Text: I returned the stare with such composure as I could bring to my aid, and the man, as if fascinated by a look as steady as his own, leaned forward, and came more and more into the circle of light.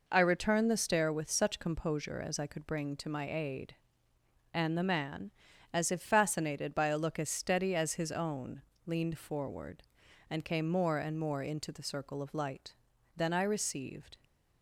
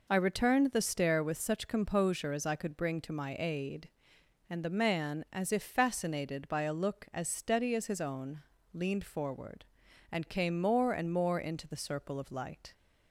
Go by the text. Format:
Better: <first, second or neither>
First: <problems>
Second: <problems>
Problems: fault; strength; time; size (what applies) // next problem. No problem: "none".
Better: second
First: goes on to say "Then I received"; noticeable; from 13.1 s on; 0.98 s long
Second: none